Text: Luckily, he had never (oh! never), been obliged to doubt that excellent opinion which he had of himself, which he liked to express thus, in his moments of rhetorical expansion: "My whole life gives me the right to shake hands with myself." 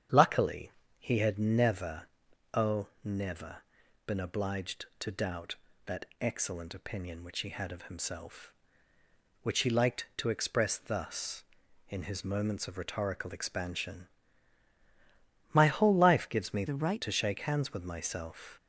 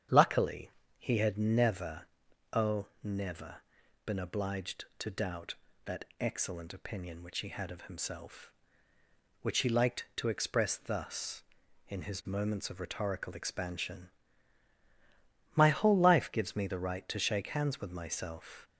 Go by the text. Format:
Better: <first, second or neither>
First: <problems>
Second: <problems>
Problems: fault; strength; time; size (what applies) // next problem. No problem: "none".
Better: second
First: starts louder than the rest; strong; until 1.3 s; 8.5 dB // pauses between "that" and "excellent"; slight; at 6.0 s; 0.16 s long // changes voice from "the" to "right"; from 16.6 to 17.0 s; 0.4 s long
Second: starts louder than the rest; strong; until 1.3 s; 8.5 dB // pauses between "that" and "excellent"; slight; at 6.0 s; 0.16 s long